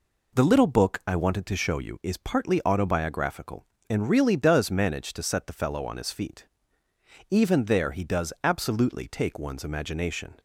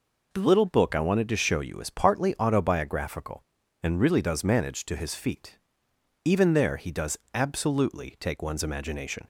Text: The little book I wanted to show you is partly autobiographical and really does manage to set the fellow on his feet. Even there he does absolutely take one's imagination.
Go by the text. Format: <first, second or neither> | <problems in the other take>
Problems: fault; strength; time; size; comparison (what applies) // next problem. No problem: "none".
first | skips "set the fellow on"; at 4.9 s // pauses between "does" and "absolutely"; slight; at 7.1 s; 0.18 s long